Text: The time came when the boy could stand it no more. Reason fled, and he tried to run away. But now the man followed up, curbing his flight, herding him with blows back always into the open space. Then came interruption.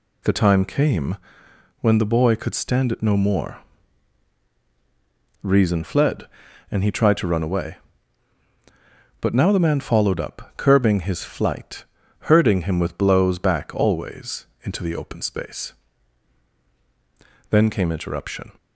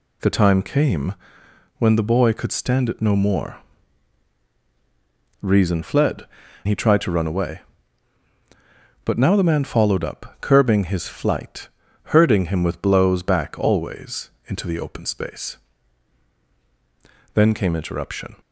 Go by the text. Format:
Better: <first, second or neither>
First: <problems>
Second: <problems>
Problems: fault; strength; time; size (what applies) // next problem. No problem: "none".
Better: first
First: pauses between "came" and "when"; noticeable; at 1.1 s; 0.64 s long // pauses between "always" and "into"; slight; at 14.4 s; 0.16 s long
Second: pauses between "came" and "when"; noticeable; at 1.1 s; 0.64 s long // skips "and"; at 6.4 s // pauses between "always" and "into"; slight; at 14.2 s; 0.16 s long